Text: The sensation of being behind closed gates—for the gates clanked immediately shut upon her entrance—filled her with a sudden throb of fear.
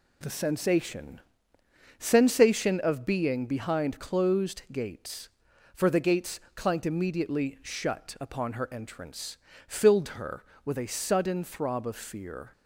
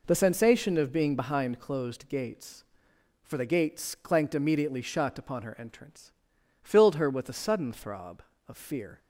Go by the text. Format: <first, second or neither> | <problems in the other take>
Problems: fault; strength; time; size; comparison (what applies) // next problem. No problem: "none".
second | says "sensation" twice; at 1.9 s